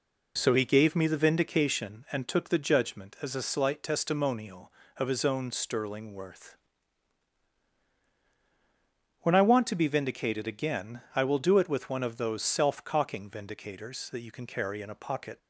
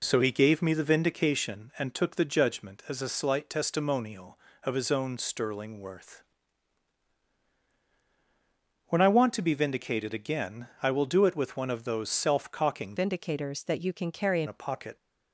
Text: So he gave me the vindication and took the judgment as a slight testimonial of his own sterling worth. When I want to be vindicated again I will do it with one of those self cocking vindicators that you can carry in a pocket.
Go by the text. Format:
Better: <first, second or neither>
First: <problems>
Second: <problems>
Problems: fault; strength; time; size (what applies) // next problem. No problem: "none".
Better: first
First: pauses between "again" and "I"; slight; at 11.0 s; 0.15 s long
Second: pauses between "again" and "I"; slight; at 10.6 s; 0.16 s long // changes voice from "vindicators" to "in"; from 12.9 to 14.4 s; 1.5 s long